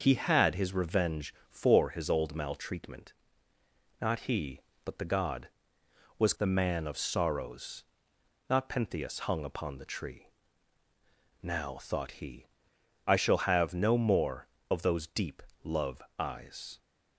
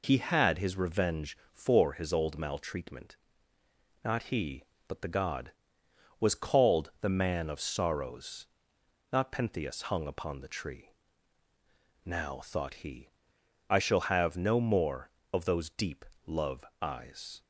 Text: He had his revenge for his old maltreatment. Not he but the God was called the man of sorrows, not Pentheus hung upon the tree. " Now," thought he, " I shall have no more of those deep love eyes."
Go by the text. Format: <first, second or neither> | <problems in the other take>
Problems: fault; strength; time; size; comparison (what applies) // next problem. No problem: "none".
second | starts louder than the rest; noticeable; until 1.0 s; 6 dB // skips "called"; at 6.3 s // pauses between "deep" and "love"; slight; at 15.4 s; 0.22 s long; slight in the second // pauses between "love" and "eyes"; slight; at 16.0 s; 0.16 s long; slight in the second